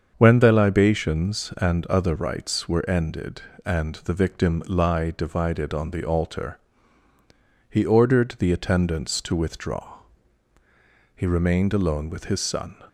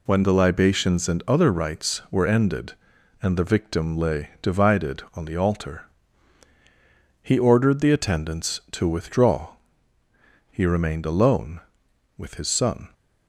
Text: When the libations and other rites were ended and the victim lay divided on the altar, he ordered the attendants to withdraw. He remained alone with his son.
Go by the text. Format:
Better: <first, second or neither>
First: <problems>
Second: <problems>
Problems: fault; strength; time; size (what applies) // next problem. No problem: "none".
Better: second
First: starts louder than the rest; until 1.1 s; 7 dB // says "lie" for "lay"; at 4.6 s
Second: none